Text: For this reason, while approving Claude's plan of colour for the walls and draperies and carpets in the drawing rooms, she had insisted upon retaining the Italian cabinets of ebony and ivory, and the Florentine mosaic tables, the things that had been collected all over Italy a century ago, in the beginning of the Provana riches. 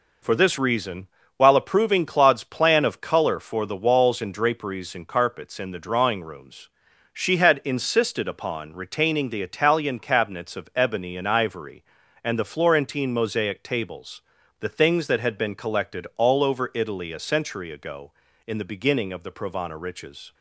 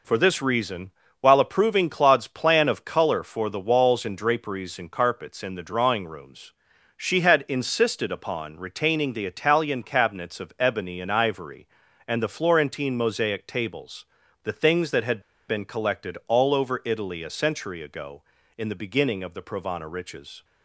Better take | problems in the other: first | pauses between "had" and "been"; slight; at 15.1 s; 0.28 s long

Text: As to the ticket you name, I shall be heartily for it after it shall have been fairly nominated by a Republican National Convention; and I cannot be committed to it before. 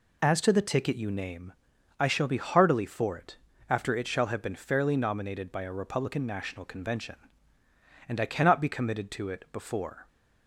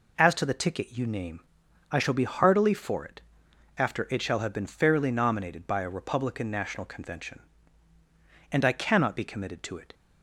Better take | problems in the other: first | pauses between "it" and "after"; noticeable; at 3.1 s; 0.58 s long; slight in the first // stops before "before"; at 9.9 s

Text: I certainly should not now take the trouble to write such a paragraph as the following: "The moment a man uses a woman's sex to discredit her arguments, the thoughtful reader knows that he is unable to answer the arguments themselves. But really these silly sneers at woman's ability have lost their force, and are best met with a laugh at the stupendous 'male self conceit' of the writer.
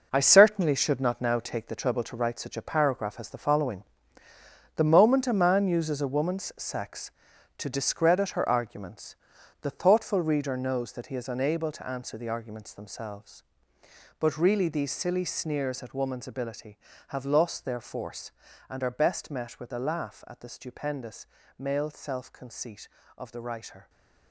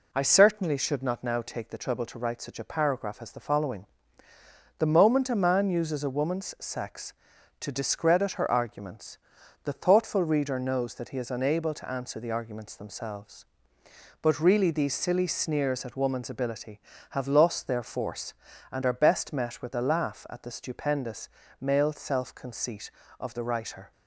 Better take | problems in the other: second | gets quieter; strong; throughout; 10.5 dB // pauses between "stupendous" and "male"; slight; at 21.2 s; 0.32 s long; slight in the second

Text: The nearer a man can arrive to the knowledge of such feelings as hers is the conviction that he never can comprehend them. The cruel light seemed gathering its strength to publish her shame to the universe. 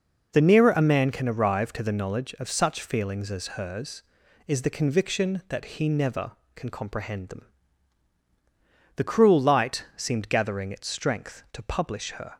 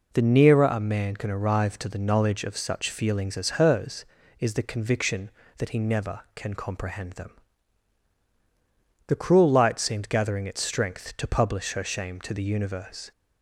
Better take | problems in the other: second | stops before "shame to the universe"; at 12.3 s

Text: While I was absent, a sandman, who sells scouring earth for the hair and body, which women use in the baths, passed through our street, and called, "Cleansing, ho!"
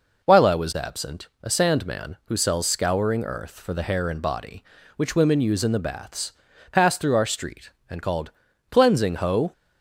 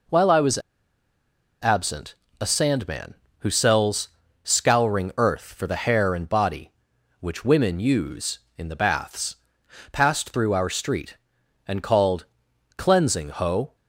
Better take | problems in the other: first | pauses between "was" and "absent"; at 0.5 s; 1.0 s long // pauses between "sells" and "scouring"; slight; at 4.0 s; 0.34 s long

